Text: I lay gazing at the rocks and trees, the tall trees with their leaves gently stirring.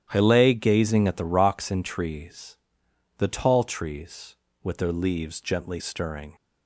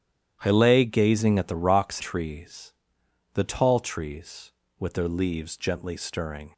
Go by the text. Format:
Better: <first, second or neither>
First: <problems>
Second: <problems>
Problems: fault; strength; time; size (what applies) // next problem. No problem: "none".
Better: first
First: starts louder than the rest; strong; until 1.1 s; 11 dB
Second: starts louder than the rest; strong; until 1.4 s; 11 dB // skips "and"; at 2.0 s